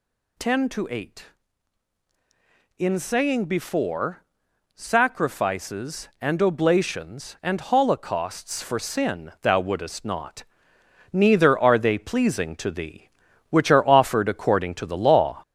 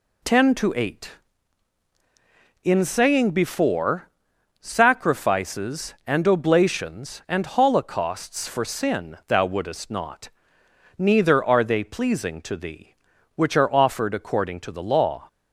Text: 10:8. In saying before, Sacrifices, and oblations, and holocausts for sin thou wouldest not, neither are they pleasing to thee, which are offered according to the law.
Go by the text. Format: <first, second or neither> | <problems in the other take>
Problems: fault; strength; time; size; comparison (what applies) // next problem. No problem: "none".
second | gets louder; slight; throughout; 3 dB